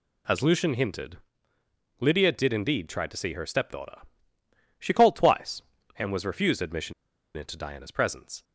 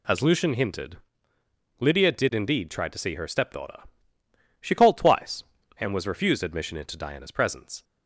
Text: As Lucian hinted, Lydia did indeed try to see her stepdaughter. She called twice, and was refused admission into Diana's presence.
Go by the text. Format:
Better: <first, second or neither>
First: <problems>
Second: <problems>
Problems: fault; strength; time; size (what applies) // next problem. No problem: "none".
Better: second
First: pauses between "admission" and "into"; at 6.9 s; 0.44 s long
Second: none